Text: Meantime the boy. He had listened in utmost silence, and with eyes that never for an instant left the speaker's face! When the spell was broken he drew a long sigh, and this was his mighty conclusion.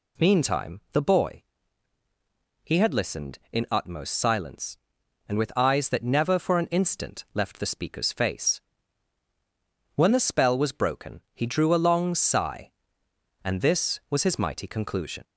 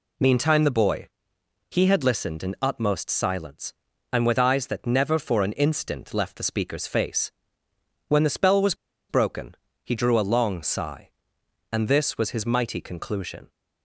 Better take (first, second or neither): first